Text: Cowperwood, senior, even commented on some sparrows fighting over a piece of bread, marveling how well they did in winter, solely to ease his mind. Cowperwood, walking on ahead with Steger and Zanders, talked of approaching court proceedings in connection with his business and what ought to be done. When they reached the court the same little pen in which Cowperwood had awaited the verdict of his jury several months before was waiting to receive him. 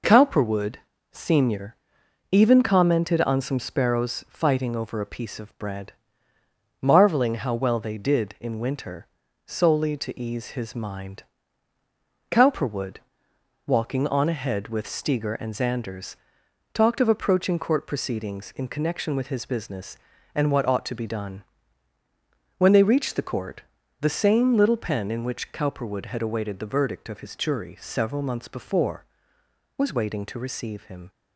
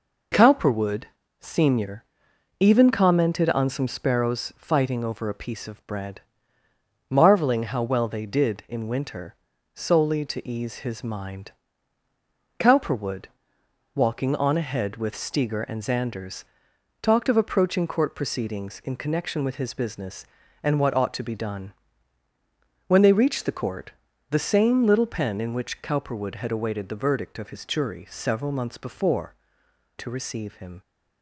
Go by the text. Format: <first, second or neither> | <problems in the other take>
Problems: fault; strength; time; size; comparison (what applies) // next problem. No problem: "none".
first | pauses between "court" and "the"; at 23.9 s; 0.40 s long; also in the first // skips "was waiting"; at 29.6 s